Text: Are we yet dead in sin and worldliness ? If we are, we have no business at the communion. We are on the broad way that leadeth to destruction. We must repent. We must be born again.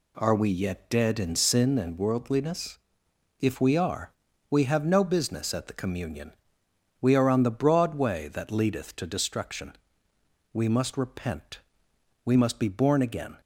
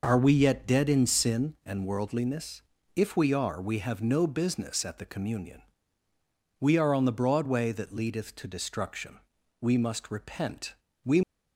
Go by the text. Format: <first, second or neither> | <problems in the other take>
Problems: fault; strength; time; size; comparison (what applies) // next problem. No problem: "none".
first | stops before "must be born again"; at 11.2 s